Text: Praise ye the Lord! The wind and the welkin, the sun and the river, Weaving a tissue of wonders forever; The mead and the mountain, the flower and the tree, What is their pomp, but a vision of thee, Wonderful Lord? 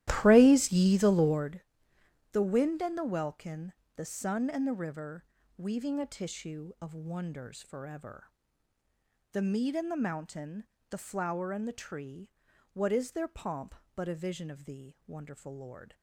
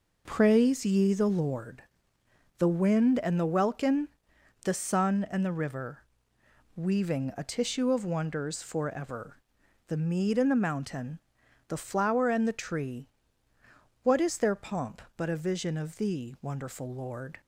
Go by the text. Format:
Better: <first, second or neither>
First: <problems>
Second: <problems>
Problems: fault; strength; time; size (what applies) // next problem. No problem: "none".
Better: second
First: starts louder than the rest; strong; until 1.6 s; 14 dB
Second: none